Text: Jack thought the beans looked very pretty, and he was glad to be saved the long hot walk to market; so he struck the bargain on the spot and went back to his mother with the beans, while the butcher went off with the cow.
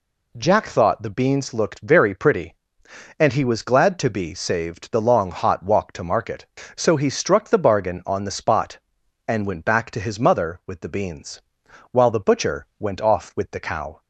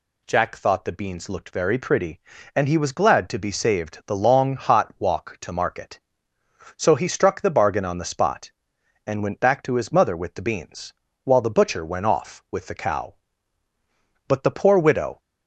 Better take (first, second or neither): first